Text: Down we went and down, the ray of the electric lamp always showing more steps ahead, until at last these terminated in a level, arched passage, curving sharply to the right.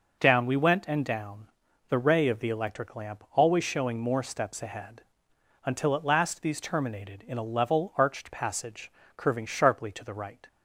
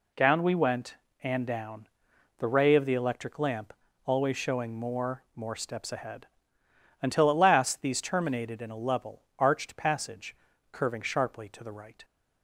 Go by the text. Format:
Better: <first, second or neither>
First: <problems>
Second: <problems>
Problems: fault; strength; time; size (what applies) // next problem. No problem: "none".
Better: first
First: none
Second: pauses between "lamp" and "always"; slight; at 3.7 s; 0.32 s long // says "more" twice; at 5.3 s